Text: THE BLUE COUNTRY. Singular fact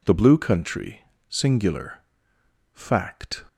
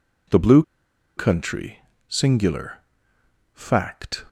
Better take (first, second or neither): first